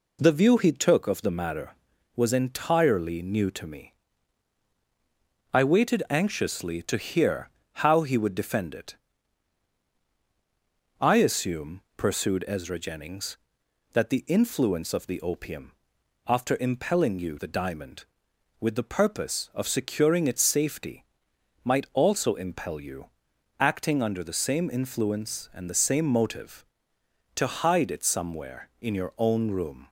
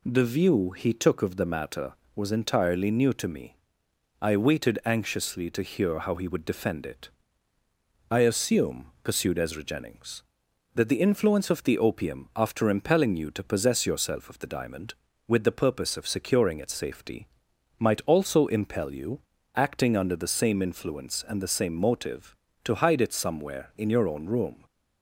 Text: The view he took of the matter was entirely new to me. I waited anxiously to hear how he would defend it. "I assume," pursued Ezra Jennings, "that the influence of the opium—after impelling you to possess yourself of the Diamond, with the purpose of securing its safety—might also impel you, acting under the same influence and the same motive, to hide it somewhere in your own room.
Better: second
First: pauses between "hear" and "how"; slight; at 7.4 s; 0.28 s long // skips "to possess yourself of"; at 17.3 s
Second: none

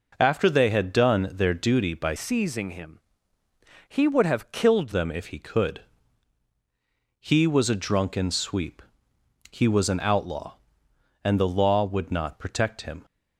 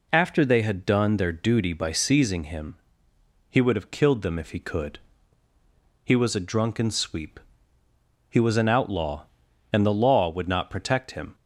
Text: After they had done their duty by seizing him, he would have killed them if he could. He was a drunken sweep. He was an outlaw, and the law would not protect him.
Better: second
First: changes voice from "seizing" to "killed"; from 2.1 to 4.9 s; 2.8 s long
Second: none

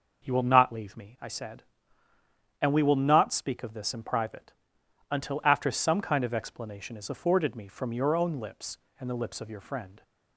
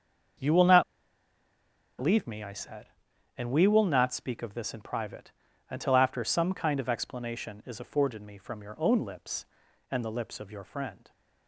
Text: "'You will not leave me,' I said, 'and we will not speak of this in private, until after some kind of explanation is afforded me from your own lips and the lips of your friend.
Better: first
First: none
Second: starts louder than the rest; until 2.5 s; 7 dB // pauses between "not" and "leave"; at 0.8 s; 1.1 s long

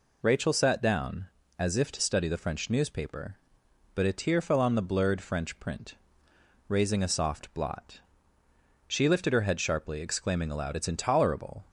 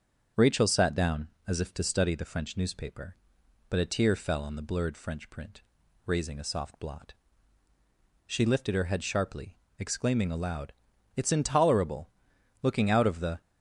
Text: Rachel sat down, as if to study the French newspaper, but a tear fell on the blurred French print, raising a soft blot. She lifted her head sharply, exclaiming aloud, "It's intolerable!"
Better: first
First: none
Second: starts louder than the rest; until 1.5 s; 7 dB // goes on to say "Looking out of the"; noticeable; from 12.6 s on; 0.78 s long

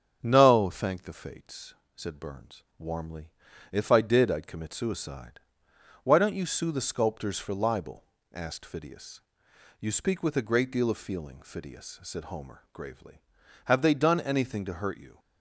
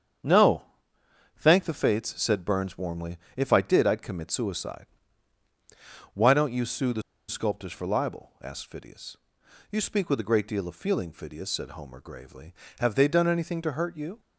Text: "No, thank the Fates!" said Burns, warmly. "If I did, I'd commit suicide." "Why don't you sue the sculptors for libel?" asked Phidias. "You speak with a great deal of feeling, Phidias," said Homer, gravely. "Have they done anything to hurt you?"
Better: first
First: starts louder than the rest; strong; until 1.2 s; 8 dB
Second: starts louder than the rest; strong; until 1.9 s; 8 dB // pauses between "the" and "sculptors"; slight; at 7.0 s; 0.27 s long

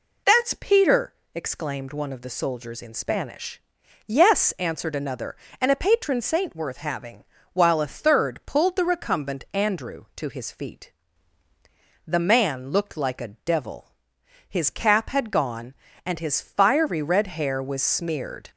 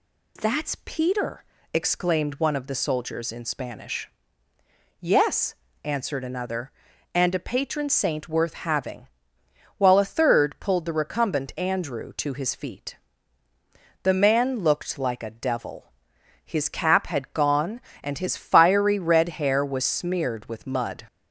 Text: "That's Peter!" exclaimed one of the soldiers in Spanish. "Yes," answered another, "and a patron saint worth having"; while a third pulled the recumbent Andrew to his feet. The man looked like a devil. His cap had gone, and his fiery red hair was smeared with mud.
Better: second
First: stops before "with mud"; at 18.5 s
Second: none

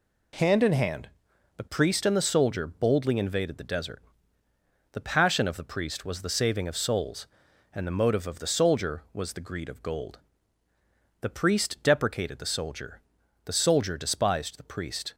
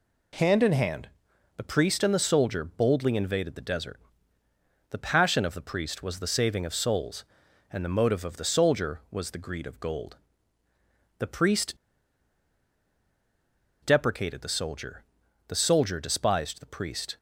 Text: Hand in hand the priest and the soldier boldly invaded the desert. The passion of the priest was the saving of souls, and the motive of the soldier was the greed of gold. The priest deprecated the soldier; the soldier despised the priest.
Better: first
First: pauses between "hand" and "the"; noticeable; at 1.1 s; 0.48 s long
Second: pauses between "hand" and "the"; noticeable; at 1.0 s; 0.48 s long // pauses between "priest" and "deprecated"; strong; at 11.7 s; 2.0 s long

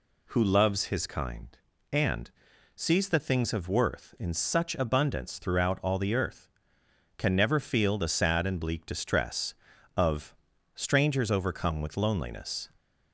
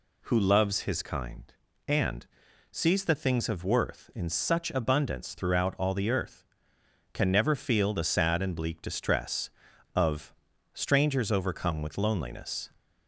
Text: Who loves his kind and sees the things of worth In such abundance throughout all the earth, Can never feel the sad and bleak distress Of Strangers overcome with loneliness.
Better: neither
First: pauses between "and" and "sees"; at 2.2 s; 0.44 s long // pauses between "Of" and "Strangers"; at 10.3 s; 0.40 s long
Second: pauses between "and" and "sees"; at 2.2 s; 0.44 s long // pauses between "Of" and "Strangers"; at 10.3 s; 0.40 s long

